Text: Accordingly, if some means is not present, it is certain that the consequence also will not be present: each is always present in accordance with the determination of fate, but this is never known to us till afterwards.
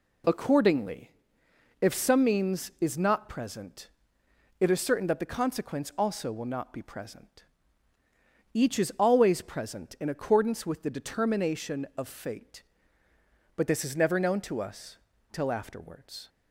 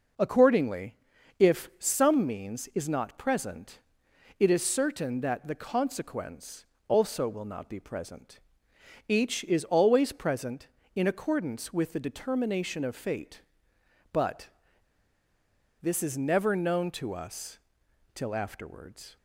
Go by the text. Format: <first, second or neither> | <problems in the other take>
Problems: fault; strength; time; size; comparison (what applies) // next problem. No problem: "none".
first | pauses between "consequence" and "also"; slight; at 6.6 s; 0.22 s long // pauses between "but" and "this"; strong; at 14.4 s; 1.3 s long // pauses between "us" and "till"; noticeable; at 17.5 s; 0.56 s long; slight in the first